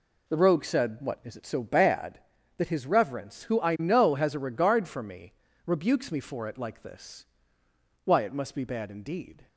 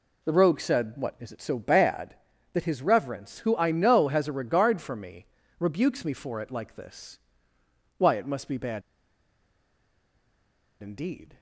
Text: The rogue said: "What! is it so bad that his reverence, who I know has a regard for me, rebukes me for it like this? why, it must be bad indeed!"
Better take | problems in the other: first | pauses between "bad" and "indeed"; strong; at 8.8 s; 2.0 s long

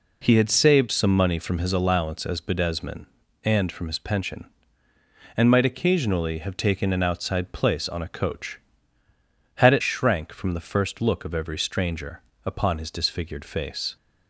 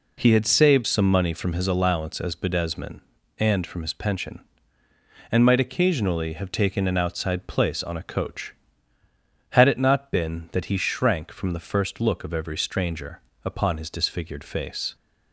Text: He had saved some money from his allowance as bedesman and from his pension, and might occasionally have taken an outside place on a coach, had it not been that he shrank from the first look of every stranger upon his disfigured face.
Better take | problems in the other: second | skips "not been that he"; at 9.8 s // pauses between "stranger" and "upon"; slight; at 12.2 s; 0.24 s long; slight in the second

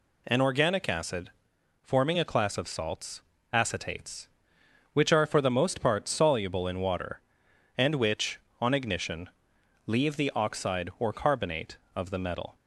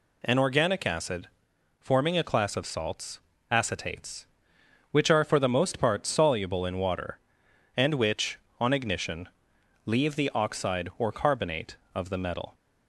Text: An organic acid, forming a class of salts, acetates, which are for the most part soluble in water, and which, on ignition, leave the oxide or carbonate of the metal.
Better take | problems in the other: neither | none

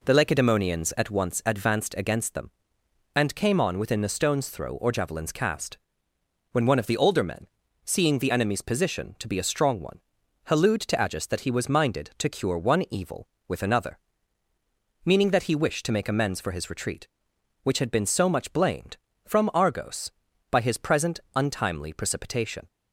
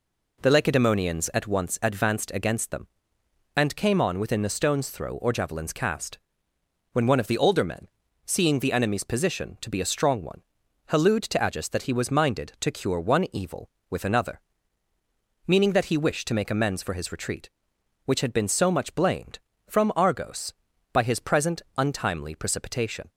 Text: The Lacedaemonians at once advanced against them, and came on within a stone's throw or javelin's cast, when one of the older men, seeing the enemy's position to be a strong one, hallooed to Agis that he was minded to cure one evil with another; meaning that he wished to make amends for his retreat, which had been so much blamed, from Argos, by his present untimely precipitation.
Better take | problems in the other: neither | pauses between "present" and "untimely"; slight; the same in both

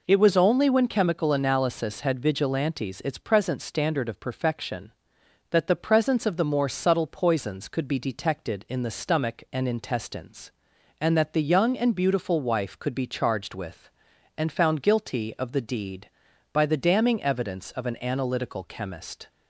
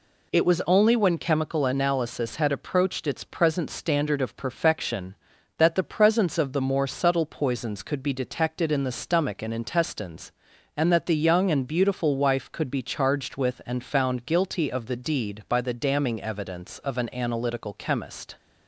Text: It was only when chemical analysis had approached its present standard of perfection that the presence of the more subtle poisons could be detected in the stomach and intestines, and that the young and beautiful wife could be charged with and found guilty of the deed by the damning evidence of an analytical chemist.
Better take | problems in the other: second | says "vigilantes" for "approached"; at 2.2 s

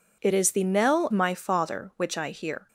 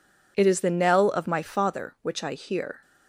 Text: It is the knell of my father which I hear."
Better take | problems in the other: second | skips "of"; at 1.0 s

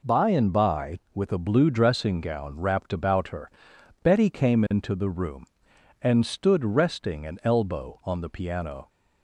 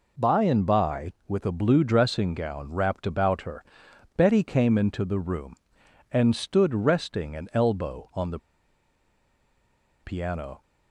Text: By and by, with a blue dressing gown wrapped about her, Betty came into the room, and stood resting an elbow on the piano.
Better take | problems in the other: first | pauses between "the" and "piano"; strong; at 8.3 s; 1.6 s long

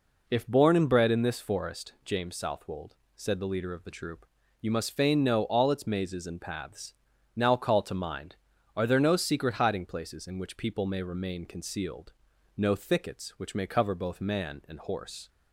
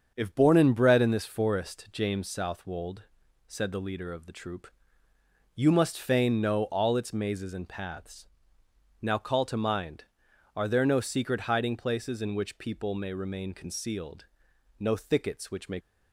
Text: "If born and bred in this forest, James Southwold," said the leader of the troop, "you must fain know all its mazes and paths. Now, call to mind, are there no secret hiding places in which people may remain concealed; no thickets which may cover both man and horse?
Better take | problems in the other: first | starts louder than the rest; until 1.1 s; 7 dB // stops before "cover both man and horse"; at 15.8 s

